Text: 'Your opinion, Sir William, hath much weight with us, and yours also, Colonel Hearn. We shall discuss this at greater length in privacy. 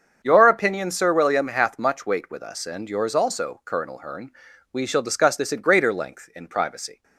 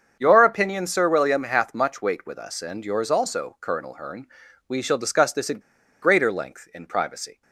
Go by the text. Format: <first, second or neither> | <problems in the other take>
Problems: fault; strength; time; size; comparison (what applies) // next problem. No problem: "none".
first | starts louder than the rest; strong; until 1.2 s; 7 dB; also in the first // pauses between "at" and "greater"; at 5.5 s; 0.42 s long